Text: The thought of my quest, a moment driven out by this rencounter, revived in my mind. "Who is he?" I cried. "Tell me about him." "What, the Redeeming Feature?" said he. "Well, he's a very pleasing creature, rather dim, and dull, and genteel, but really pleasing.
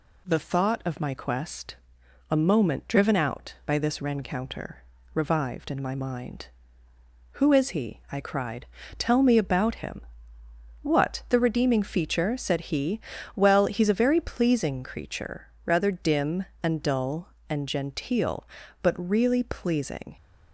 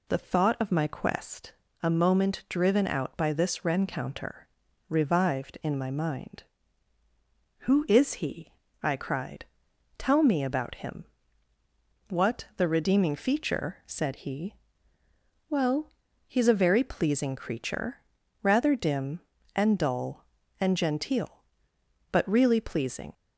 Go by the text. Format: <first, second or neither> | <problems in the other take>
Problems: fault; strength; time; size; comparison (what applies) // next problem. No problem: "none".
first | starts louder than the rest; slight; until 1.4 s; 2.5 dB